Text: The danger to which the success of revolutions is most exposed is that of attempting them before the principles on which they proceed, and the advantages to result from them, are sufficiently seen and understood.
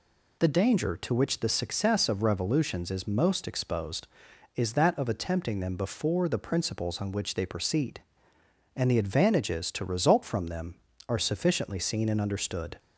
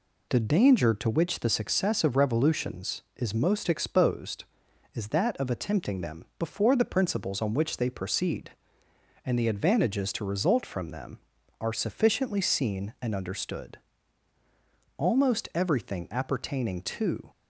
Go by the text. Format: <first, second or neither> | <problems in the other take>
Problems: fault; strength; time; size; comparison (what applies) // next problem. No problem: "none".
first | goes on to say "Almost everything appertaining to"; strong; from 14.9 s on; 2.2 s long